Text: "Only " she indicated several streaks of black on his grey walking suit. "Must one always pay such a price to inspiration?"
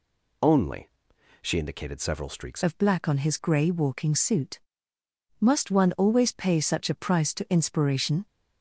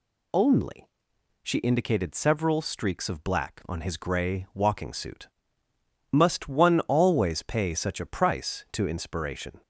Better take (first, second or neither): second